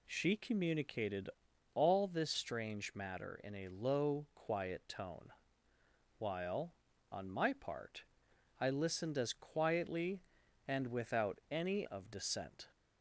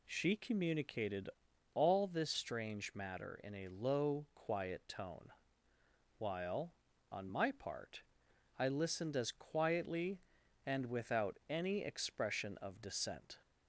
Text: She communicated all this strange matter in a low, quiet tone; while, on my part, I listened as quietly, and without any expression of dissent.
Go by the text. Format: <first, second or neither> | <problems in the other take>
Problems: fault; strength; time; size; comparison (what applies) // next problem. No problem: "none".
second | pauses between "communicated" and "all"; noticeable; at 1.2 s; 0.46 s long; noticeable in the second // skips "expression"; at 11.8 s